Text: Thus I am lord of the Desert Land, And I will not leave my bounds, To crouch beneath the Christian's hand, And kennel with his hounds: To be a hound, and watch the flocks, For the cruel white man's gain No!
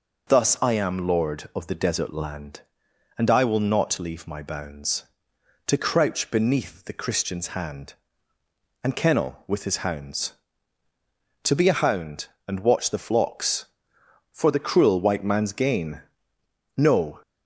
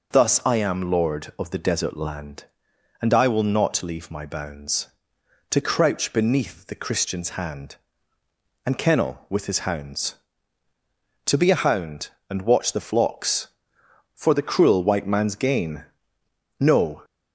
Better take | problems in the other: neither | pauses between "gain" and "No"; noticeable; the same in both

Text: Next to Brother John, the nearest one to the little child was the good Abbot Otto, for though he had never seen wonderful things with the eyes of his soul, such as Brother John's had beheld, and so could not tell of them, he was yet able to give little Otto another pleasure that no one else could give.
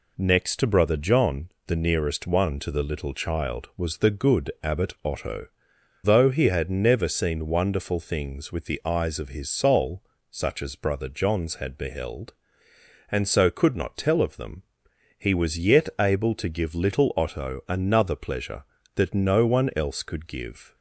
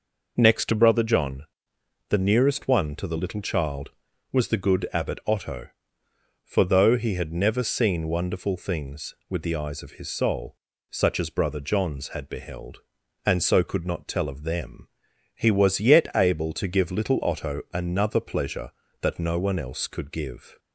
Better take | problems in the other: second | skips "for"; at 5.7 s

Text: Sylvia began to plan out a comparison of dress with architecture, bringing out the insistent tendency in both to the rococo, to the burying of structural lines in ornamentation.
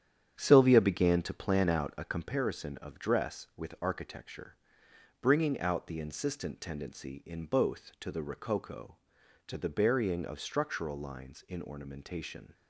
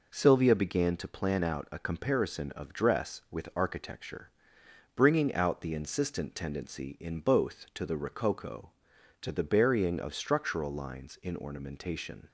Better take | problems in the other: second | starts louder than the rest; strong; until 2.3 s; 9 dB

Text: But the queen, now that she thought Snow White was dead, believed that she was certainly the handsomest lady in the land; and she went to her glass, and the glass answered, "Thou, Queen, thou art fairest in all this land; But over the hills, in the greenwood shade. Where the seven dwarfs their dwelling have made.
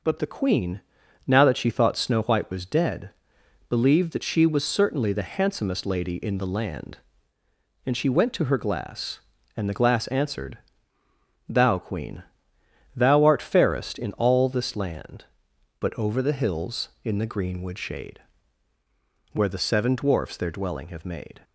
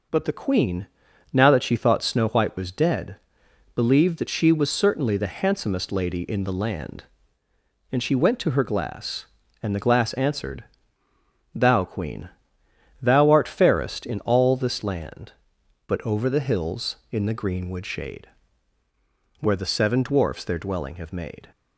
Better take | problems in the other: neither | none

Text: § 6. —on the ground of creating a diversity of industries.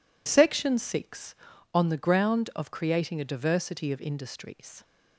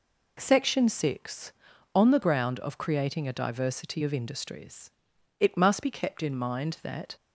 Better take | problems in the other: first | goes on to say "It must be kept in mind that"; strong; from 5.4 s on; 1.7 s long

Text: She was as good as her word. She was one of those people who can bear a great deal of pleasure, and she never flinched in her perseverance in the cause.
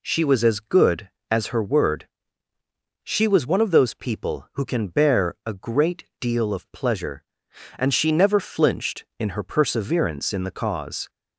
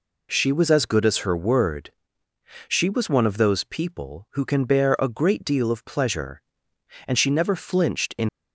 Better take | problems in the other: first | stops before "her perseverance in the cause"; at 8.2 s

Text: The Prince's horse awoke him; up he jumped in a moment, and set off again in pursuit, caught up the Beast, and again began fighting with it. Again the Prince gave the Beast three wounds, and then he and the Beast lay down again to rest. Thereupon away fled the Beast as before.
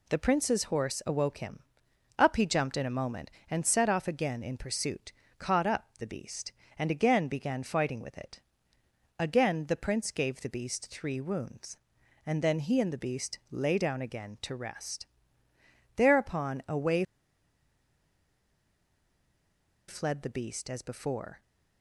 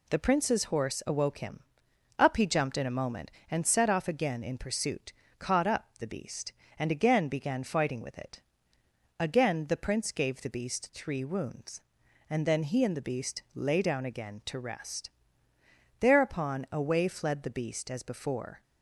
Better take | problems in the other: second | pauses between "away" and "fled"; strong; at 17.0 s; 2.8 s long

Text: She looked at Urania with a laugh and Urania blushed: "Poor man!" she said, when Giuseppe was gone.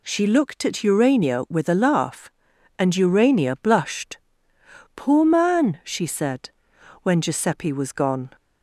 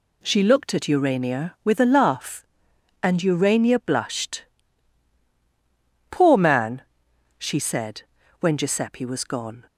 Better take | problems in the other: neither | none

